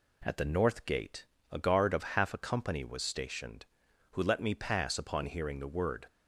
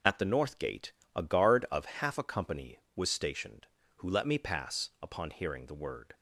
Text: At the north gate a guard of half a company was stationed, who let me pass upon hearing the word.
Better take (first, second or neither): neither